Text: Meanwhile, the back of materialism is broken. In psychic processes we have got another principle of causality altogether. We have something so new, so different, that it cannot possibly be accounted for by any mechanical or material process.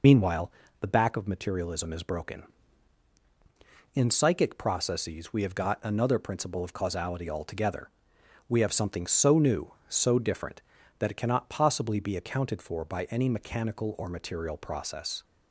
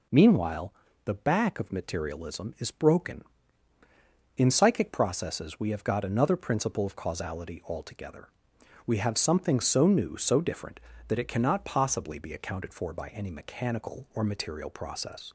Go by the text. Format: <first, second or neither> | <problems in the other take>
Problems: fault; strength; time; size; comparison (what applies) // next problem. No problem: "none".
second | loses the start of "Meanwhile"; at 0.0 s; 50 ms